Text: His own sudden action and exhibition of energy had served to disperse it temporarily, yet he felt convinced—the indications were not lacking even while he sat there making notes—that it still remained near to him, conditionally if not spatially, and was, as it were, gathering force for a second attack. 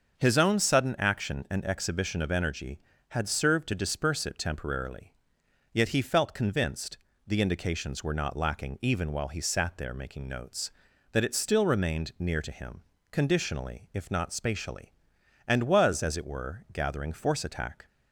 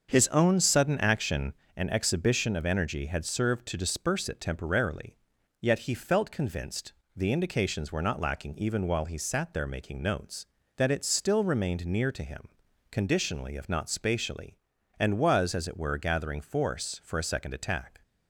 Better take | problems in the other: second | starts louder than the rest; until 1.2 s; 6.5 dB; also in the second // skips "for a second"; at 17.4 s

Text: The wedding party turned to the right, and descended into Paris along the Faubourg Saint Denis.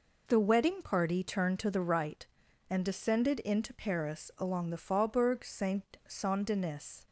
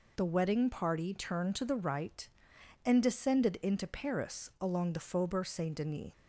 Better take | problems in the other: second | says "Saint" twice; at 6.0 s

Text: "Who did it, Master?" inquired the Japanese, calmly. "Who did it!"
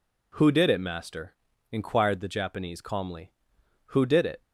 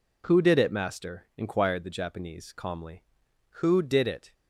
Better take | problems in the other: neither | none

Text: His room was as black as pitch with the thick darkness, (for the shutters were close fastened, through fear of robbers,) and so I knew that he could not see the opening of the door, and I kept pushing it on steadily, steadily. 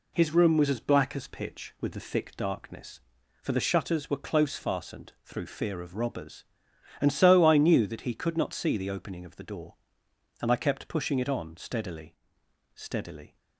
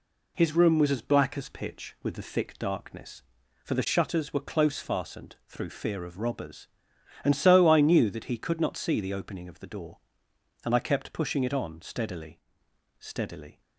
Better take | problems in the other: neither | none

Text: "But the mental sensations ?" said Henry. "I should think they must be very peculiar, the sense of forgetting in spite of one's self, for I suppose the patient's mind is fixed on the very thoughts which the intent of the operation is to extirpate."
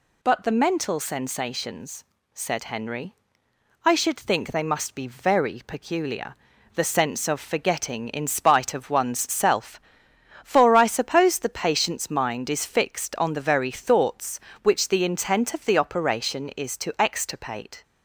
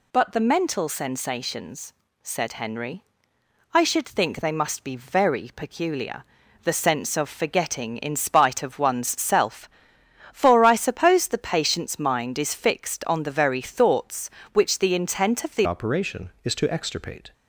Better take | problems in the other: first | changes voice at "operation"; from 15.6 s on; 1.7 s long

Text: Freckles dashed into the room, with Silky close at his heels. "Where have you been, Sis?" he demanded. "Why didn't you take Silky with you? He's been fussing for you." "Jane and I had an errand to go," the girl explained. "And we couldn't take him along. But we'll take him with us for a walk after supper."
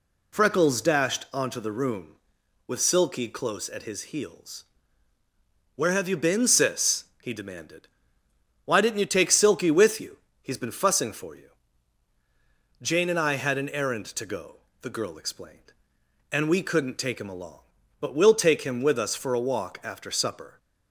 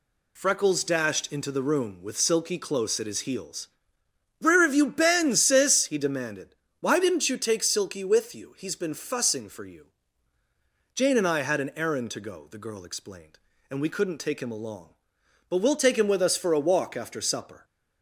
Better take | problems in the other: second | says "onto" for "into"; at 1.3 s

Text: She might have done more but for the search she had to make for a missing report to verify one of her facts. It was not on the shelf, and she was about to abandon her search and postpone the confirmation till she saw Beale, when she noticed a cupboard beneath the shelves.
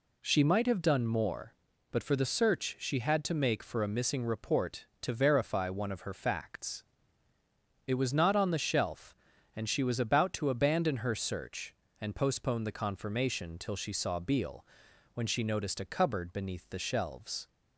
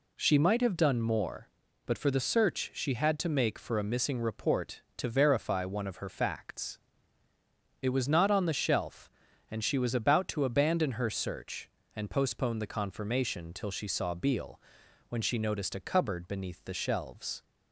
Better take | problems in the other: neither | none

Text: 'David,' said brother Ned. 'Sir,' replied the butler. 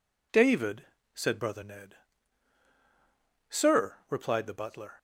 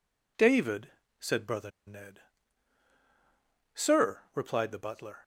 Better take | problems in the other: first | pauses between "brother" and "Ned"; slight; at 1.7 s; 0.15 s long

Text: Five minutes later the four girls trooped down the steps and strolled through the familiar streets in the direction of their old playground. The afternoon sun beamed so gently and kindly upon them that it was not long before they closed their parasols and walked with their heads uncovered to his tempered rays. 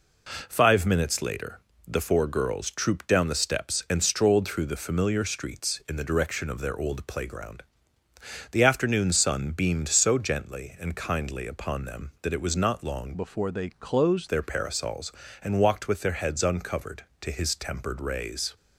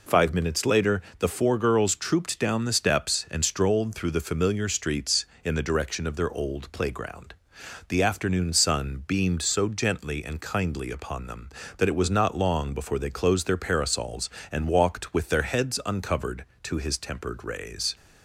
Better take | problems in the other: second | pauses between "later" and "the"; slight; at 1.5 s; 0.30 s long; slight in the second // changes voice from "before" to "closed"; from 13.1 to 14.2 s; 1.1 s long

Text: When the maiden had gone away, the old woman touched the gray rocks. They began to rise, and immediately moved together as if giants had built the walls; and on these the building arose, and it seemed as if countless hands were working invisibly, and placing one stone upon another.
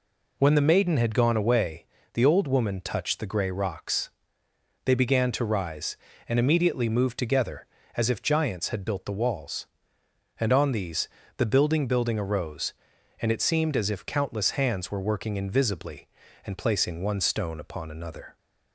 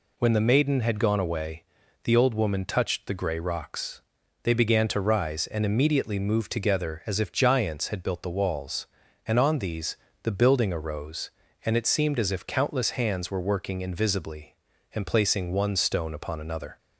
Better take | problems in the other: second | pauses between "these" and "the"; slight; at 11.0 s; 0.30 s long; slight in the second // says "building" twice; at 11.8 s

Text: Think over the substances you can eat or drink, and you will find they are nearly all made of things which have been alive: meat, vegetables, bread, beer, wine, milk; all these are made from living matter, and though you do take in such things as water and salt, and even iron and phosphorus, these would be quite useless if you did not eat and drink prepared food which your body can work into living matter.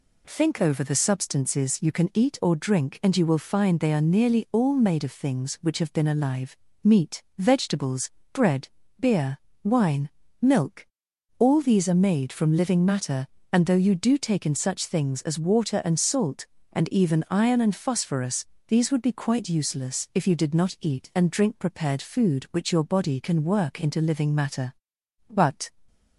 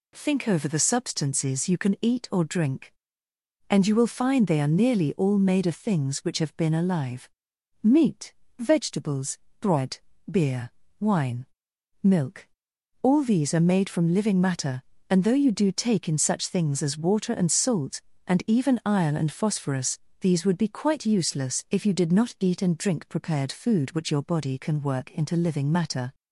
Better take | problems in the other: second | goes on to say "But"; slight; from 25.2 s on; 0.40 s long

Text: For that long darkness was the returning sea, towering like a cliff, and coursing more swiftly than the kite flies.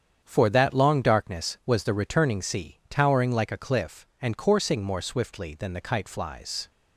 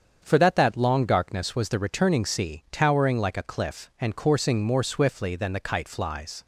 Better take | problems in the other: first | starts louder than the rest; strong; until 1.2 s; 7.5 dB; strong in the first // says "that" twice; at 0.5 s

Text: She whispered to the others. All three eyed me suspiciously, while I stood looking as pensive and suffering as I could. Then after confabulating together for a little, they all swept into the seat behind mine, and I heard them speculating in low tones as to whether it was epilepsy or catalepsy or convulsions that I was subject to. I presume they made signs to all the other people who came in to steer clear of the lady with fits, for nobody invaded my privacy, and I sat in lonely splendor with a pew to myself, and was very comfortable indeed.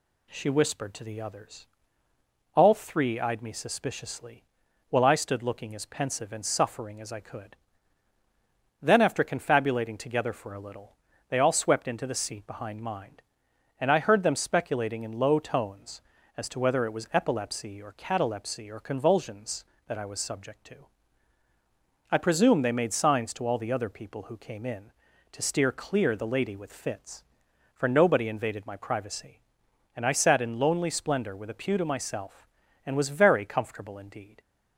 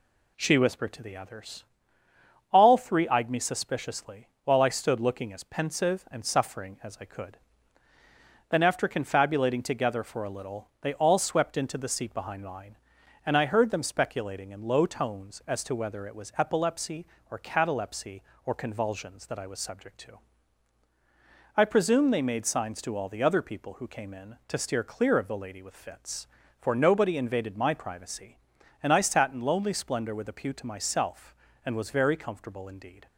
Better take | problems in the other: second | skips "of"; at 26.1 s

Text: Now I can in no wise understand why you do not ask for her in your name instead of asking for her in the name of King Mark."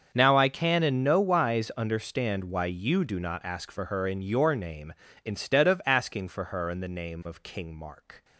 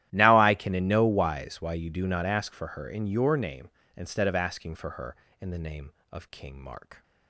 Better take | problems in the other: first | starts louder than the rest; strong; until 1.1 s; 13 dB; also in the first // skips "understand"; at 1.5 s

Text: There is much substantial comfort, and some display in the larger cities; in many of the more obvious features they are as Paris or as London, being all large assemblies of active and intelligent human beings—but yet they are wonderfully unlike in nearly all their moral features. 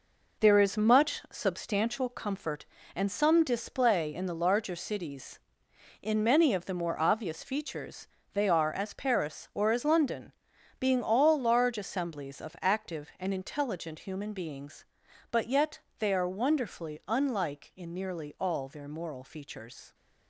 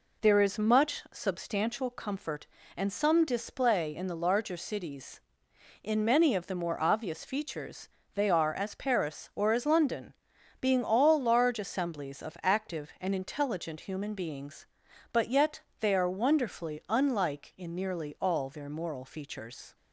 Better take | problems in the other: second | gets quieter; strong; throughout; 7.5 dB // pauses between "features" and "they"; slight; at 8.0 s; 0.28 s long; slight in the second // pauses between "yet" and "they"; slight; at 15.7 s; 0.22 s long; slight in the second

